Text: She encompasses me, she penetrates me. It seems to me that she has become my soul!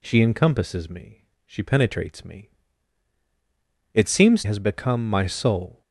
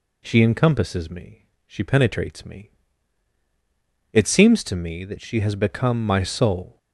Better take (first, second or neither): second